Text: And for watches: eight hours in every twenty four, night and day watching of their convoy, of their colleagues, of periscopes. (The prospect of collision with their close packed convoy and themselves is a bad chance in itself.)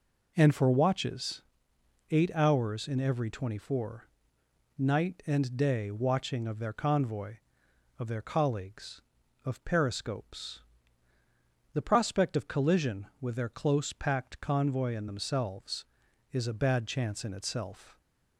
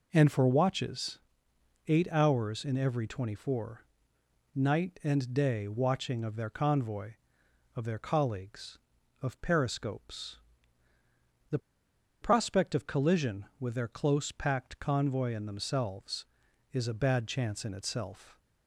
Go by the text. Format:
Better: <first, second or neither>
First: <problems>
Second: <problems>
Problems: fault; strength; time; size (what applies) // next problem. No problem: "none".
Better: first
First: none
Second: pauses between "The" and "prospect"; noticeable; at 11.5 s; 0.63 s long